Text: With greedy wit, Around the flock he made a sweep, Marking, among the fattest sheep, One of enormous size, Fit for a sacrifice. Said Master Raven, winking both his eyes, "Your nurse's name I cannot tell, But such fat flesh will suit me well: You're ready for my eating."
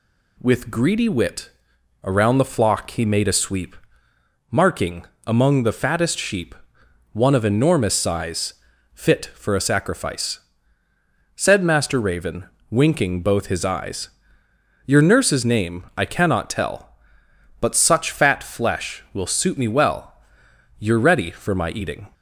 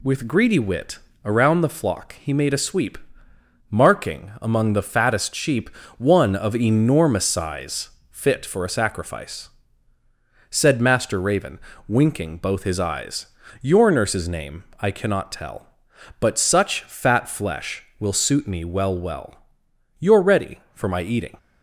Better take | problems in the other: first | pauses between "name" and "I"; slight; at 14.6 s; 0.18 s long // says "well" twice; at 18.9 s

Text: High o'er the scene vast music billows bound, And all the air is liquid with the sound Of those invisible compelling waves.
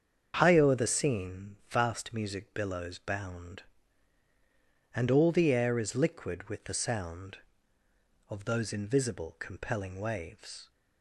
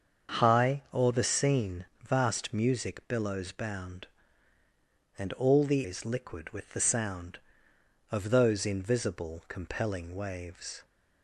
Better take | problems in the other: first | starts louder than the rest; until 1.4 s; 7 dB; strong in the first // pauses between "scene" and "vast"; slight; at 1.8 s; 0.18 s long // skips "air"; at 5.8 s

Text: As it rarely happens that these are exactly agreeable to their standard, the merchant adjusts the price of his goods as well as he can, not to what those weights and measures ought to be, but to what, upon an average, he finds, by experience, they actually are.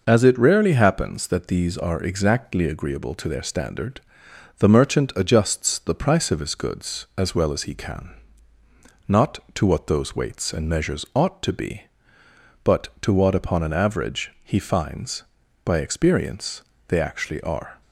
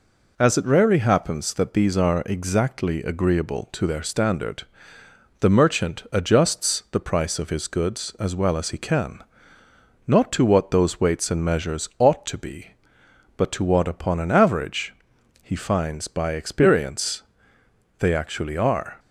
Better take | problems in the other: neither | none

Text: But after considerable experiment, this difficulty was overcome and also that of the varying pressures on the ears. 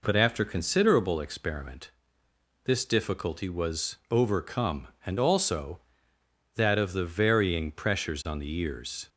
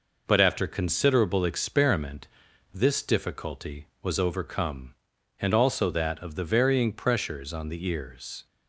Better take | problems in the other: neither | none

